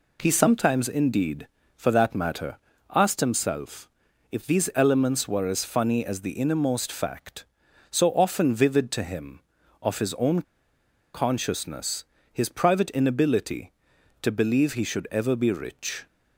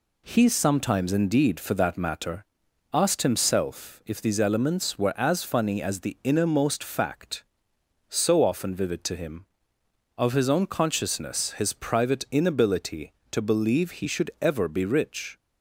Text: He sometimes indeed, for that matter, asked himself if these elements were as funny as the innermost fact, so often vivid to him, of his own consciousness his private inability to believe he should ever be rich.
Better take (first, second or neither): second